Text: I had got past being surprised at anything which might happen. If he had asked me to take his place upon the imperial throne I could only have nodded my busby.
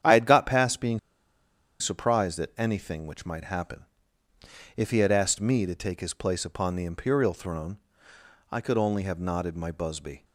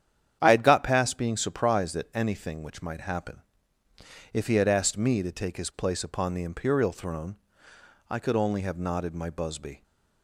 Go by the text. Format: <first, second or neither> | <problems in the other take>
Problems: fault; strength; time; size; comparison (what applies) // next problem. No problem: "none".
second | starts louder than the rest; strong; until 1.8 s; 9.5 dB; strong in the second // pauses between "being" and "surprised"; noticeable; at 0.9 s; 0.82 s long // pauses between "throne" and "I"; noticeable; at 7.7 s; 0.72 s long; noticeable in the second